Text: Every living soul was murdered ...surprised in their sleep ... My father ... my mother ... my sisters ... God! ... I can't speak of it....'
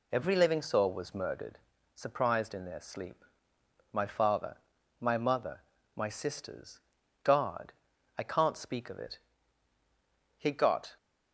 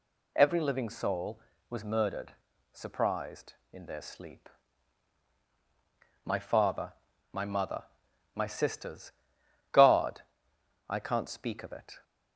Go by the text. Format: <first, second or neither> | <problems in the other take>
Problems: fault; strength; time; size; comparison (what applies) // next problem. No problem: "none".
second | goes on to say "He got"; from 10.3 s on; 0.58 s long